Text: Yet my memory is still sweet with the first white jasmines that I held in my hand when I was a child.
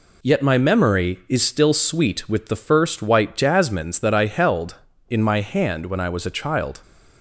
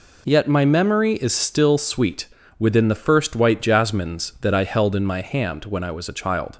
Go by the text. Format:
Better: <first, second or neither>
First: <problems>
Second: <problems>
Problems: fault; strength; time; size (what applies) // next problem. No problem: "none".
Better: first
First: none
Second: says "within" for "with"; at 2.5 s